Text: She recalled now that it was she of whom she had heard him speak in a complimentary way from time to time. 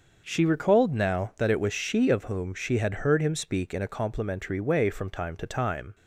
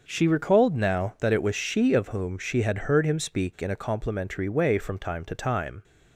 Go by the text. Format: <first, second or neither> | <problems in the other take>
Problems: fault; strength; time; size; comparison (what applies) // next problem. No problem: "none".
neither | starts louder than the rest; the same in both